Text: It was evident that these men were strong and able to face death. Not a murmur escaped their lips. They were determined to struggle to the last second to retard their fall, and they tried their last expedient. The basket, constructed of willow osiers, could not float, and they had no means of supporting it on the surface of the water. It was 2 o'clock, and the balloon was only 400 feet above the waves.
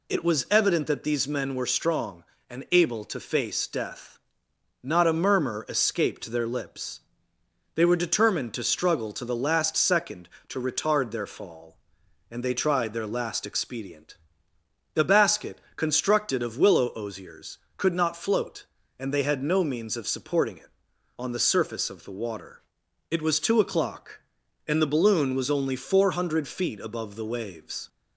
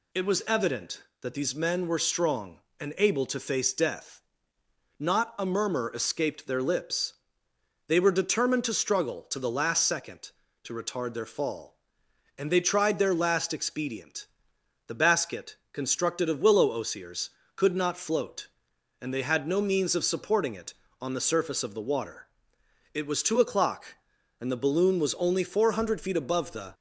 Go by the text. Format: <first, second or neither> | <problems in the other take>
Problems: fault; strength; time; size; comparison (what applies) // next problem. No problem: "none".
first | stops before "waves"; at 26.7 s